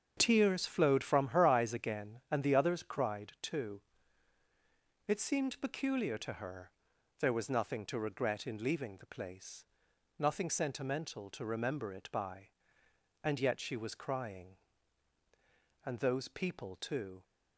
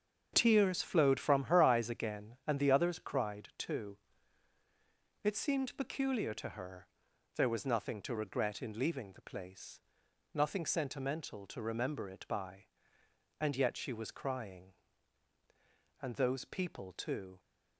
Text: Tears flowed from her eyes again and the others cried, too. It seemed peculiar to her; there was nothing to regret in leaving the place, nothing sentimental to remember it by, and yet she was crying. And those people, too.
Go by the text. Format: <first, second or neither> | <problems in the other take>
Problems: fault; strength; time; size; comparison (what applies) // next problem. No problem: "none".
neither | starts louder than the rest; strong; the same in both